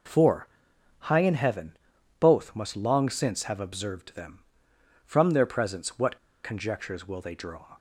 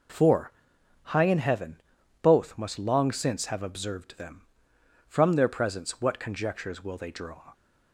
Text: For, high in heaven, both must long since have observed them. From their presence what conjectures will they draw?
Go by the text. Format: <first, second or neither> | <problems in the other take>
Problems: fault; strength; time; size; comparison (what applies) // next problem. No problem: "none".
second | pauses between "what" and "conjectures"; slight; at 6.1 s; 0.26 s long